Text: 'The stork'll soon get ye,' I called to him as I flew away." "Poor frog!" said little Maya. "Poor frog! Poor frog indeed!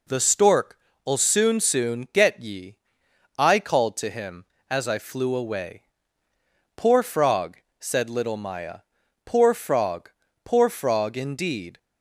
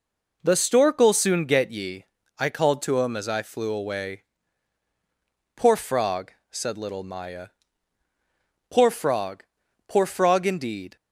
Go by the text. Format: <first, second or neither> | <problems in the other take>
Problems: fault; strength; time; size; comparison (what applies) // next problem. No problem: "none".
second | says "soon" twice; at 1.5 s